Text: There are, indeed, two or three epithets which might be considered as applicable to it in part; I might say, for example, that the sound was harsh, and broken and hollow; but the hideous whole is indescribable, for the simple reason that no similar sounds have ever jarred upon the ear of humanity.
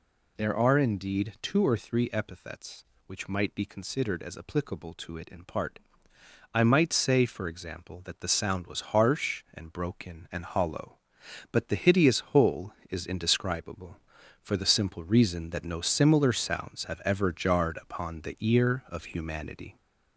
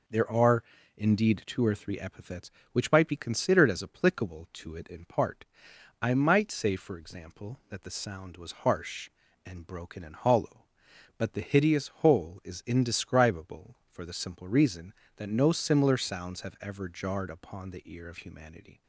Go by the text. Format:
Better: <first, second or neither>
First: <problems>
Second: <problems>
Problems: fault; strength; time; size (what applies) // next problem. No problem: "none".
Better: second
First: gets louder; slight; throughout; 3 dB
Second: none